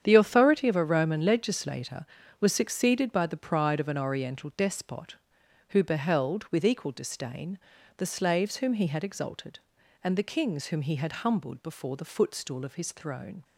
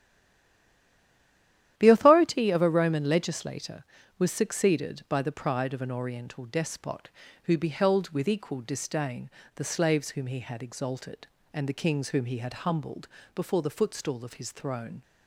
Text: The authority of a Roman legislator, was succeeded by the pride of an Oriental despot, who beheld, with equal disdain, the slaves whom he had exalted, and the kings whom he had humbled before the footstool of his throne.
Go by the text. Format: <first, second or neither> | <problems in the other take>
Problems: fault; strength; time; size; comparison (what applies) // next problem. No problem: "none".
first | stays silent before the first word; noticeable; until 1.7 s; 1.7 s long // starts louder than the rest; strong; until 2.8 s; 11.5 dB; strong in the first // pauses between "humbled" and "before"; slight; at 13.0 s; 0.26 s long